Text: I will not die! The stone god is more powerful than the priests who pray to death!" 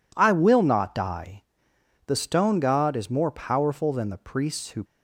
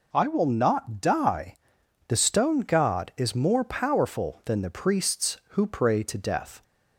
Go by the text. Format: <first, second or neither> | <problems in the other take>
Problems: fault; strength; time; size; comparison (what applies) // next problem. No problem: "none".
second | stops before "pray to death"; at 4.8 s